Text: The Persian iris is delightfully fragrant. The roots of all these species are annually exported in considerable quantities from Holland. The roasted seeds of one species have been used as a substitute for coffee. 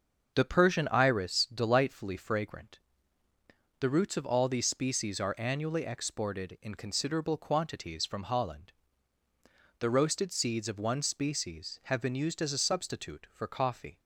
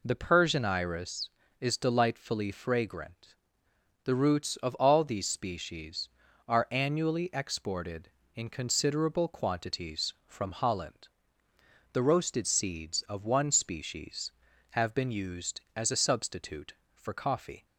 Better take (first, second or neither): second